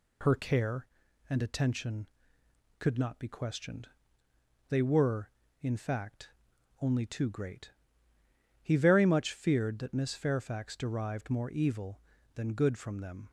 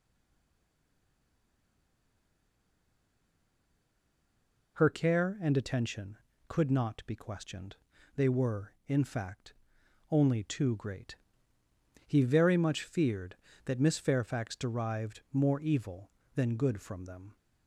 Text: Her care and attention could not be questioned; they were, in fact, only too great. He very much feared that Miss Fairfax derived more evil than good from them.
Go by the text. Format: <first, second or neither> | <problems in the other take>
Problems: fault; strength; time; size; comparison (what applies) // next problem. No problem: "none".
first | stays silent before the first word; strong; until 4.7 s; 4.7 s long